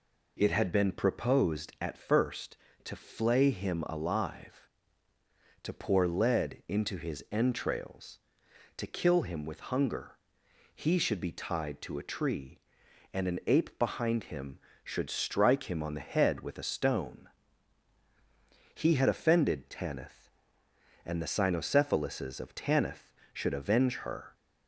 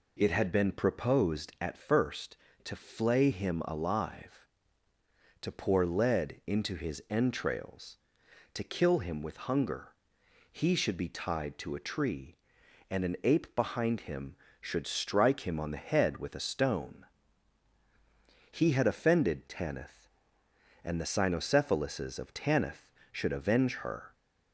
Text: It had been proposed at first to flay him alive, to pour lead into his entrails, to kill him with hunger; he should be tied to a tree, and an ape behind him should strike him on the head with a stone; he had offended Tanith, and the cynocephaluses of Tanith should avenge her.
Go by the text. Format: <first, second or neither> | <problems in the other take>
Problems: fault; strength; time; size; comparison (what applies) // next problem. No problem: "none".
neither | none